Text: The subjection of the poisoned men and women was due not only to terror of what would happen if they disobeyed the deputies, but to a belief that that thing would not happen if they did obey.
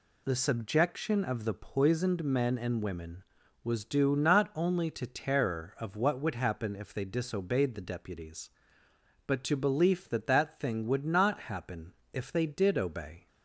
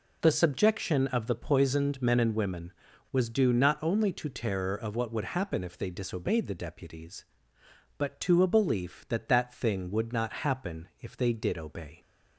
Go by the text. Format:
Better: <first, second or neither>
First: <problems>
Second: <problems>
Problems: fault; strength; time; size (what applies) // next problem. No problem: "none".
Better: second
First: skips "a"; at 9.5 s // pauses between "happen" and "if"; slight; at 11.9 s; 0.22 s long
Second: none